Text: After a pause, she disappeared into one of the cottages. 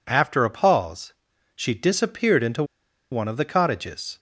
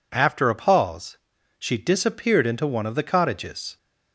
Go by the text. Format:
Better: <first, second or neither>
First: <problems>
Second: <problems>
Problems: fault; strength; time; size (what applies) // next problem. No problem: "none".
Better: second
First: pauses between "into" and "one"; noticeable; at 2.6 s; 0.48 s long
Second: none